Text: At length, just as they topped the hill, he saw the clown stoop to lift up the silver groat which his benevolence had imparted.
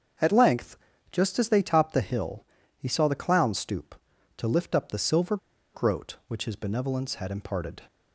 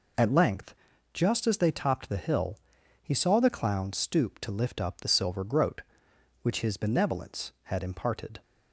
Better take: second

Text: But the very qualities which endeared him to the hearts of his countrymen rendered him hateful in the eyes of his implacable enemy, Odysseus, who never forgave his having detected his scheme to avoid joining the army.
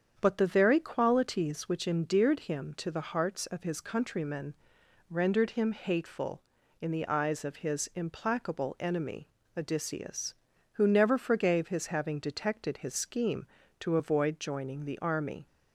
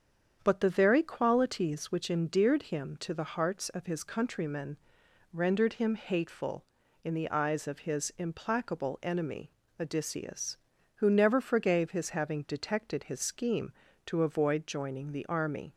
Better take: neither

